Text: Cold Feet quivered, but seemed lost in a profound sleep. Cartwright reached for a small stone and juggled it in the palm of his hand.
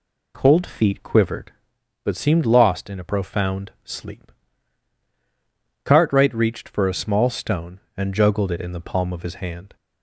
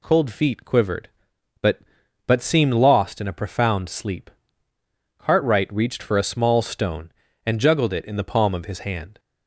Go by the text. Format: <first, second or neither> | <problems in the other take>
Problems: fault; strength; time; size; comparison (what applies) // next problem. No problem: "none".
first | says "but" twice; at 2.2 s